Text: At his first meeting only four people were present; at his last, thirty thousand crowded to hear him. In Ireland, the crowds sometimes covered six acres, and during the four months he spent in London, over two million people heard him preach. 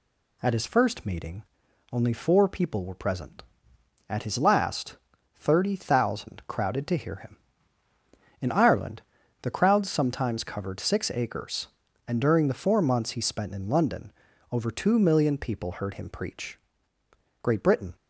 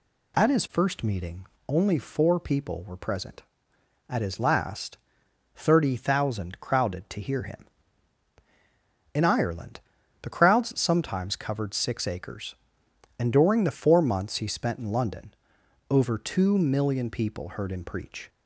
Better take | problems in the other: second | pauses between "meeting" and "only"; noticeable; at 1.4 s; 0.48 s long; slight in the second // goes on to say "Great Britain"; from 17.4 s on; 0.50 s long

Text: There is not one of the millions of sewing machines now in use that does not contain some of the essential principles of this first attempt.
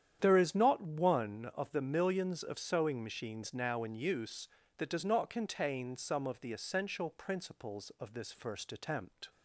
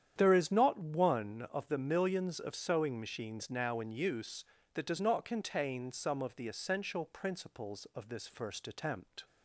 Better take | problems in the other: neither | starts louder than the rest; strong; the same in both

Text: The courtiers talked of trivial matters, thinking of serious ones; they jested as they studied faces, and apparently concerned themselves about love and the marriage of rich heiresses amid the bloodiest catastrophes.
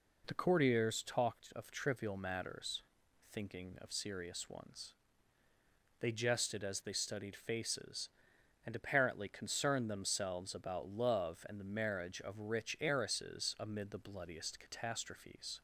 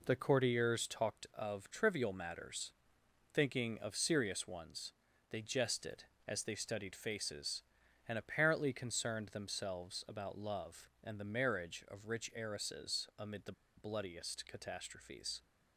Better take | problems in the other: first | pauses between "the" and "bloodiest"; slight; at 13.5 s; 0.25 s long

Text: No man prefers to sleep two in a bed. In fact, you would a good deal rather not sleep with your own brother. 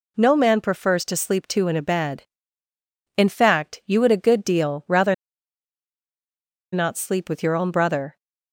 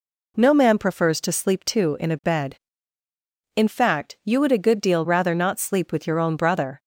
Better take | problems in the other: second | pauses between "rather" and "not"; strong; at 5.1 s; 1.5 s long

